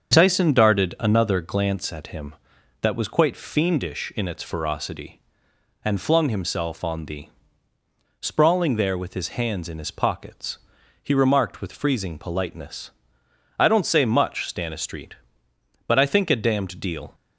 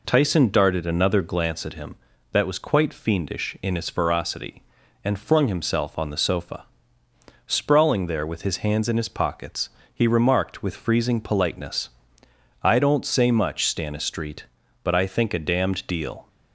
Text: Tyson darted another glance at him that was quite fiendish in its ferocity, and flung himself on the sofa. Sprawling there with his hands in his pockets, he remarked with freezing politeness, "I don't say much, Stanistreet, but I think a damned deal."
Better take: second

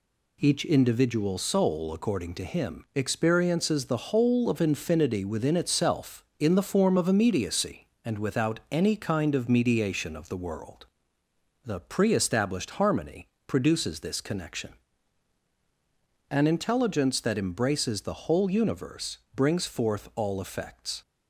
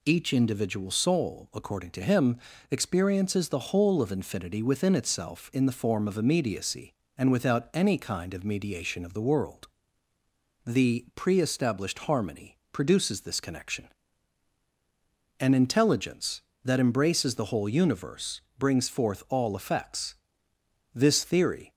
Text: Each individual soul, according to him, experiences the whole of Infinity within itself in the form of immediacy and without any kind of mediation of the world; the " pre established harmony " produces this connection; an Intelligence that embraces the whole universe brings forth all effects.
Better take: first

